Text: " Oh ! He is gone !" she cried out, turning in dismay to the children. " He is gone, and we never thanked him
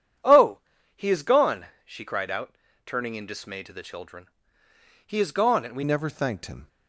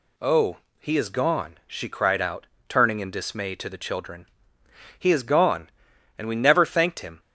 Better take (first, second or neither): second